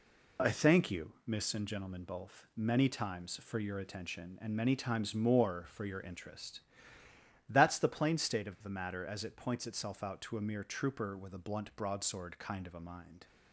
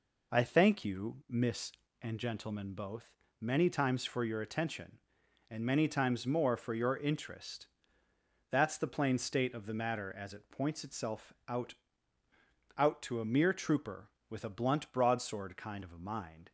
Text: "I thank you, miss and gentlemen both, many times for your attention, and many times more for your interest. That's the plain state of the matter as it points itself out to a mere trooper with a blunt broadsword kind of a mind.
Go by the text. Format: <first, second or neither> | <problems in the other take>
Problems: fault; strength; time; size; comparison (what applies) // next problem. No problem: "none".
first | says "out" twice; at 12.7 s